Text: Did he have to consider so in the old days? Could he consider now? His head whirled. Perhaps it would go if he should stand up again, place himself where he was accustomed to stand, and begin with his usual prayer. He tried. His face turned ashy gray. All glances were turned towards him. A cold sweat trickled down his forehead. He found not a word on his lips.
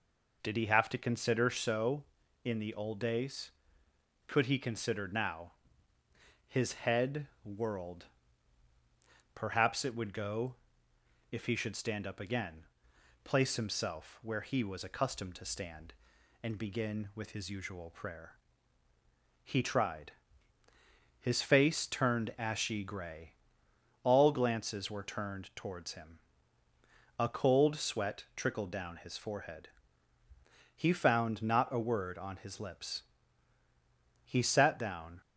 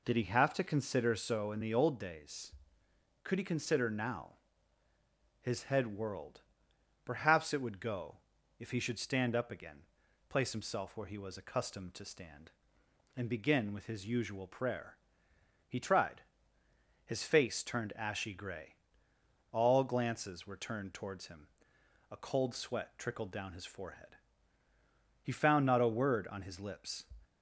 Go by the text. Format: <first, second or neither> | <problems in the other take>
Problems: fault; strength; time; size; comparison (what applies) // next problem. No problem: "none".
second | pauses between "head" and "whirled"; slight; at 7.2 s; 0.18 s long // pauses between "go" and "if"; noticeable; at 10.5 s; 0.76 s long; also in the second // goes on to say "He sat down"; noticeable; from 34.2 s on; 0.96 s long